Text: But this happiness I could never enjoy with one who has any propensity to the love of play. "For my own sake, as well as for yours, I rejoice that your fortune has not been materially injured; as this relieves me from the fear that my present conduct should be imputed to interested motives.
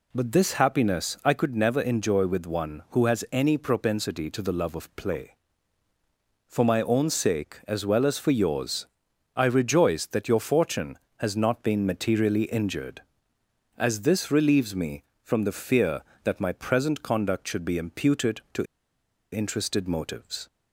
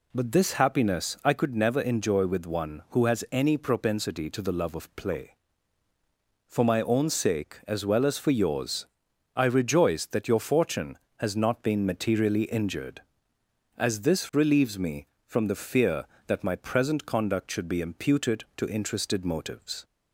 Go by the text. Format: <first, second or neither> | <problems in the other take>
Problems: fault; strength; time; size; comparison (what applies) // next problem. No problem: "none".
second | pauses between "to" and "interested"; noticeable; at 18.6 s; 0.66 s long